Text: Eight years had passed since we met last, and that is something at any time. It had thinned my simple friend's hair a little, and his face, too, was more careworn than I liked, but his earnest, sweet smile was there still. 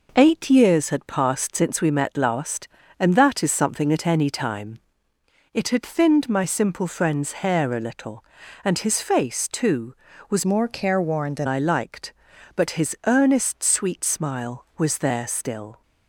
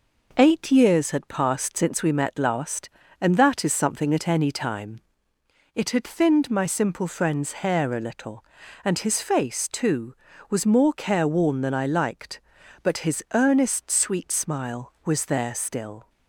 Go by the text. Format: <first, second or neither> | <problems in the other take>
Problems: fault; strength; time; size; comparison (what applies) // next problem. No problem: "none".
second | changes voice from "more" to "than"; from 10.4 to 11.4 s; 1.0 s long